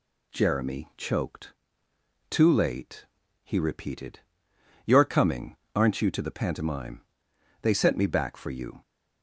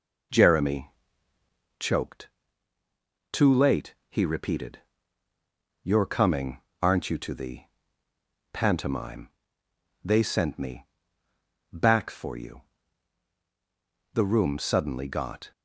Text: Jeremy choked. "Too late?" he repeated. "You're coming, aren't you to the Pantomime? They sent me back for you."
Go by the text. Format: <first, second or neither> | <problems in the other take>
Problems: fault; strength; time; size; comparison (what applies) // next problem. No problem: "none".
first | pauses between "Jeremy" and "choked"; noticeable; at 0.8 s; 0.88 s long // pauses between "the" and "Pantomime"; noticeable; at 7.6 s; 0.86 s long // pauses between "me" and "back"; noticeable; at 10.8 s; 0.86 s long // goes on to say "The room suddenly got"; from 14.1 s on; 1.3 s long